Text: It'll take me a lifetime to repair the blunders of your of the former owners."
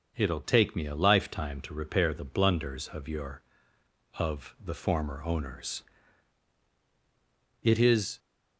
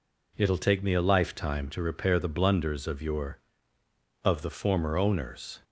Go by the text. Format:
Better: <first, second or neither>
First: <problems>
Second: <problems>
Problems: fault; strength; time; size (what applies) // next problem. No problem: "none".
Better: second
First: starts louder than the rest; until 1.1 s; 6 dB // goes on to say "It is"; from 7.6 s on; 0.56 s long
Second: none